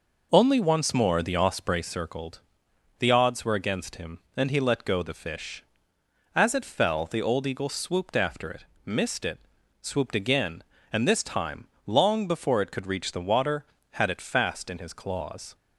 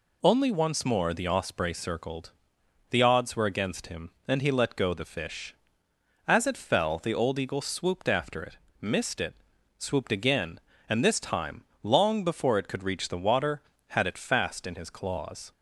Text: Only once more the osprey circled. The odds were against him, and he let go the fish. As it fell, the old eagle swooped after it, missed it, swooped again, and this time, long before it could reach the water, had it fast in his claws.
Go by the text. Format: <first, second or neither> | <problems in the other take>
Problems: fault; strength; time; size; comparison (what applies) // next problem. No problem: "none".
second | starts louder than the rest; noticeable; until 1.9 s; 5 dB